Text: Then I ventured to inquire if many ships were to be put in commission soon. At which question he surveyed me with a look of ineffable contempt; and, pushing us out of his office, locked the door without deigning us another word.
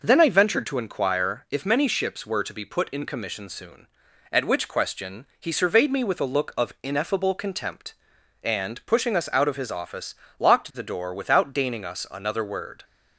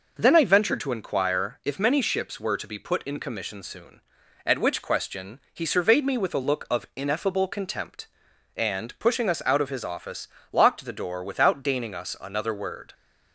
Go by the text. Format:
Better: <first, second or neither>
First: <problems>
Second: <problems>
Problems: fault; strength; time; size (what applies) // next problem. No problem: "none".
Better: neither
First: none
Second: none